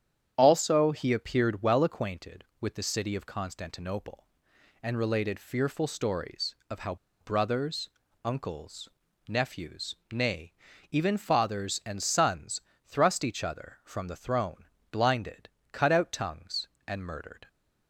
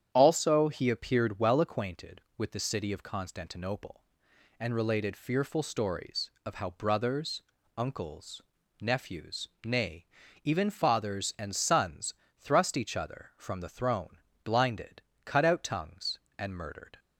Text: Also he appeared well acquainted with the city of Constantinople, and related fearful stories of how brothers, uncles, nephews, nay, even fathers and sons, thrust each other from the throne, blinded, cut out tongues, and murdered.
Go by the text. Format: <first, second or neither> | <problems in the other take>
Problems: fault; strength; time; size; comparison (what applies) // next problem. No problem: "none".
second | starts louder than the rest; strong; until 1.3 s; 9 dB; strong in the second // pauses between "how" and "brothers"; slight; at 6.9 s; 0.25 s long